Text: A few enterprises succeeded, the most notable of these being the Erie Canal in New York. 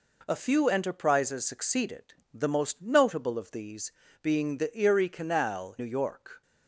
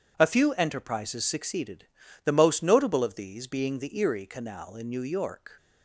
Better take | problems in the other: second | pauses between "these" and "being"; slight; at 3.8 s; 0.32 s long // skips "in"; at 5.7 s

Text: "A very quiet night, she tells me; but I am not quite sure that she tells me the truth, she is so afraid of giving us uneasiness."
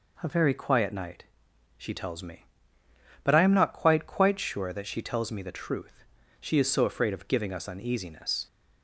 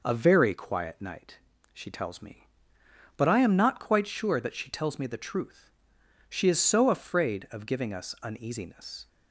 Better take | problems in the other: second | says "quite" twice; at 4.0 s

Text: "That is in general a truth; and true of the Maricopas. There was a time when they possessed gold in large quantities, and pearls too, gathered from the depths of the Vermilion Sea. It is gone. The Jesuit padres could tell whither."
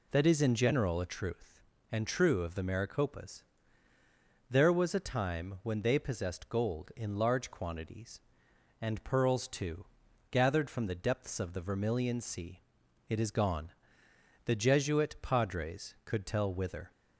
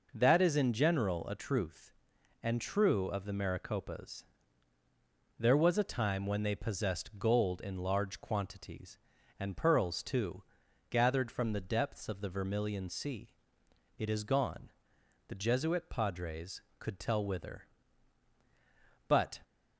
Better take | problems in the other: first | goes on to say "But"; slight; from 19.0 s on; 0.34 s long

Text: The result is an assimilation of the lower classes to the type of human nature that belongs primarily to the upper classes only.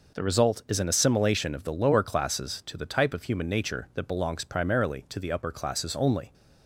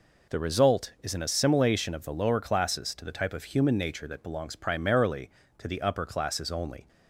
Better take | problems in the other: neither | none

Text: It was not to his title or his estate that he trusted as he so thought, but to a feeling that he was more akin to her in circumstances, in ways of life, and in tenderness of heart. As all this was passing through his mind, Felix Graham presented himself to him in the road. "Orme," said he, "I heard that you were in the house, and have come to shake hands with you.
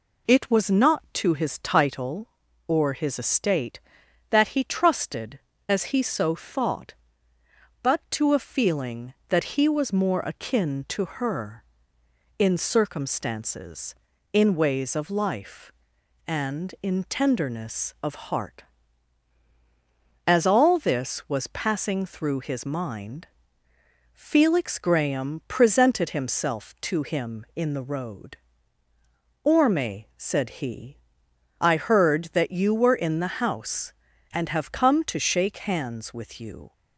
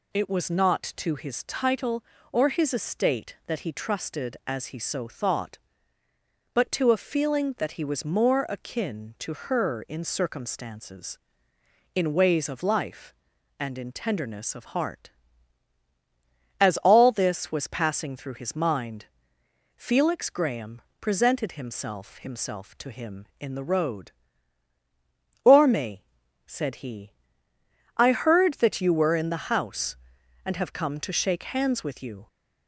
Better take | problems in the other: first | pauses between "Graham" and "presented"; slight; at 20.8 s; 0.18 s long // says "himself" twice; at 22.1 s

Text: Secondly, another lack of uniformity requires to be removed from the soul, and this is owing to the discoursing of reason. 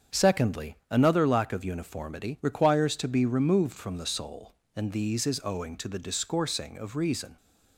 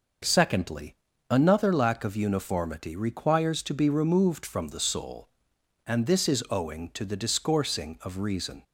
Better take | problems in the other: second | starts louder than the rest; strong; until 1.2 s; 7.5 dB // says "these" for "this"; at 4.9 s

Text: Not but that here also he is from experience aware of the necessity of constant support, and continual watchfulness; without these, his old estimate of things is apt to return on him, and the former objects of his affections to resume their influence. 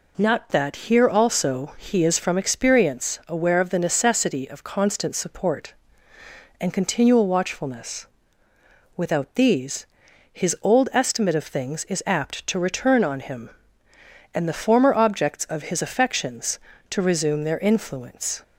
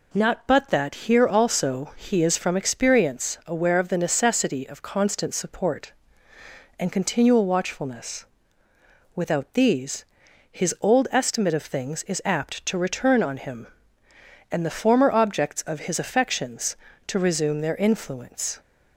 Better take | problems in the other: second | skips "but"; at 0.4 s

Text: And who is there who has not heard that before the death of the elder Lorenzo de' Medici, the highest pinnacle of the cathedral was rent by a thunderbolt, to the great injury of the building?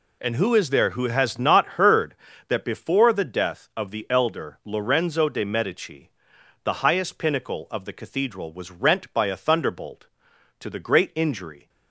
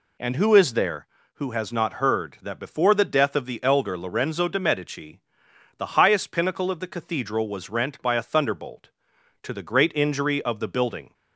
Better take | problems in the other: second | stops before "of the building"; at 11.6 s

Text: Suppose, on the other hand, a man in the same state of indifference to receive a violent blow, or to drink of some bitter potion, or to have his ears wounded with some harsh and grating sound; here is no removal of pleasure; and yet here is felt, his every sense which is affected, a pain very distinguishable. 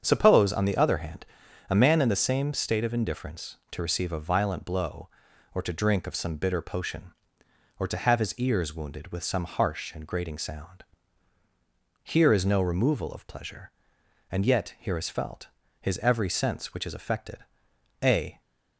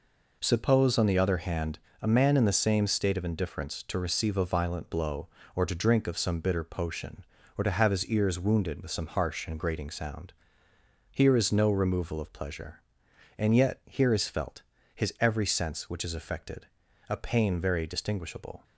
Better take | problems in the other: second | starts louder than the rest; strong; until 1.0 s; 7.5 dB // stops before "pain very distinguishable"; at 18.4 s

